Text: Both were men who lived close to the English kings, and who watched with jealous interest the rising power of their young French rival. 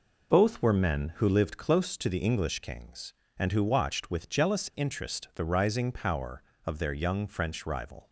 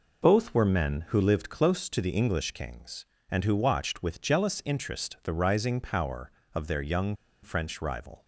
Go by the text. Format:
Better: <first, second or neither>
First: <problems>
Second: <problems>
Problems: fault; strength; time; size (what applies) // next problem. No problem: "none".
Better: first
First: none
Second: pauses between "young" and "French"; slight; at 7.1 s; 0.29 s long